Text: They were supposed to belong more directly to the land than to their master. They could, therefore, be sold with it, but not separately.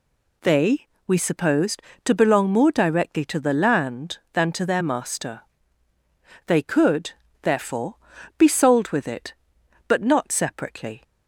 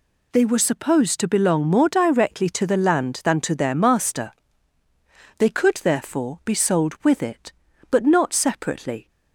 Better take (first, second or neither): second